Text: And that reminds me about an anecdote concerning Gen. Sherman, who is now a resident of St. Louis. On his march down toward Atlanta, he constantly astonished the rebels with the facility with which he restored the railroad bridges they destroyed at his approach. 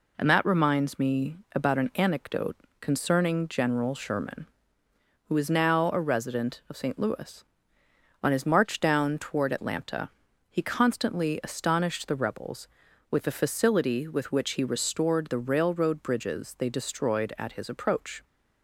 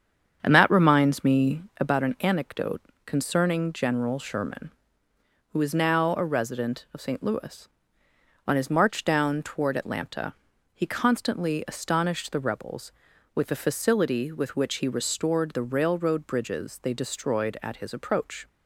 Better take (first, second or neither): first